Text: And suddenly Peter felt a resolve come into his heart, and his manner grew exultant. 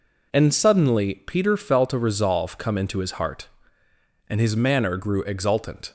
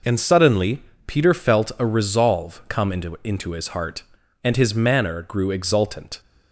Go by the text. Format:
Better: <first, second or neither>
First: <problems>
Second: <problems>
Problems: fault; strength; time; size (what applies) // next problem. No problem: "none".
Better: first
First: none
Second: pauses between "suddenly" and "Peter"; slight; at 0.8 s; 0.24 s long // says "into" twice; at 3.2 s